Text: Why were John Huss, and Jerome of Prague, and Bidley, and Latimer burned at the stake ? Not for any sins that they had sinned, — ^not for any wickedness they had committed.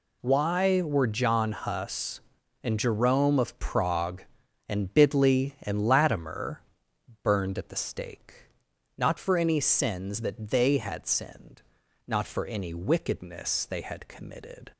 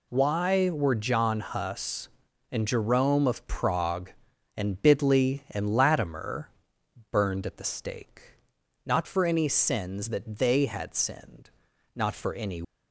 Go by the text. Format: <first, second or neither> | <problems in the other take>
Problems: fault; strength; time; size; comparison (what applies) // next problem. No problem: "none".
first | pauses between "Latimer" and "burned"; noticeable; at 6.4 s; 0.64 s long; noticeable in the first // stops before "wickedness they had committed"; at 12.6 s